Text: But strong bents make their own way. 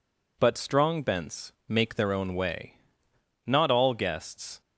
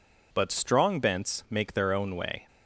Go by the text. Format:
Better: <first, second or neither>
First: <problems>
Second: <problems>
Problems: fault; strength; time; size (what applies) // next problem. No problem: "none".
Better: second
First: pauses between "bents" and "make"; slight; at 1.5 s; 0.16 s long // goes on to say "Not all guests"; noticeable; from 3.4 s on; 1.1 s long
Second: none